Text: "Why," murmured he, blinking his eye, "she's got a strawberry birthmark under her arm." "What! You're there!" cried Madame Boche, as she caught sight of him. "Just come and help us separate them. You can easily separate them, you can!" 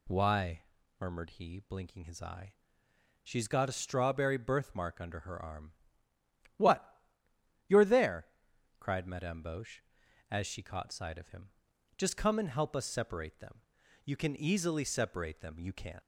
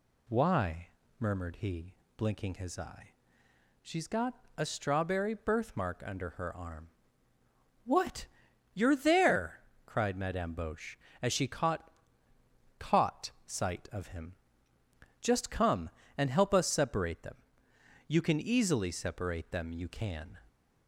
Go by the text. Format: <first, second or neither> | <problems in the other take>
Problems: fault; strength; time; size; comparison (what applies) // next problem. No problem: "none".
first | says "caught" twice; at 12.7 s